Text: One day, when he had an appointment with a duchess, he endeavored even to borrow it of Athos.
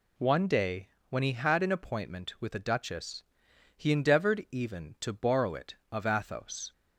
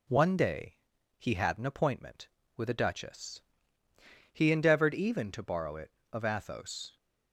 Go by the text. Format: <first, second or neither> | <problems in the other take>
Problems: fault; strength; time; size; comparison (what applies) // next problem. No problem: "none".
first | skips "when"; at 0.9 s